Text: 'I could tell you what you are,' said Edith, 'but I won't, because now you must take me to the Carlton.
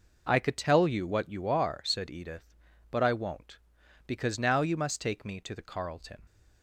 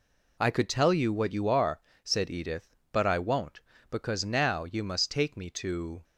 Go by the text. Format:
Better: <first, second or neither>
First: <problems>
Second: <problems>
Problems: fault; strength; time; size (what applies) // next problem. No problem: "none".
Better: first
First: none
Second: stops before "the Carlton"; at 6.0 s